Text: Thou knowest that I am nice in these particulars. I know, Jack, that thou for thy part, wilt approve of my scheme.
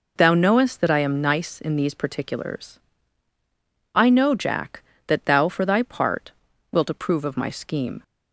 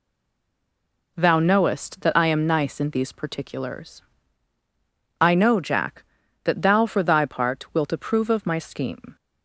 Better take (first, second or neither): first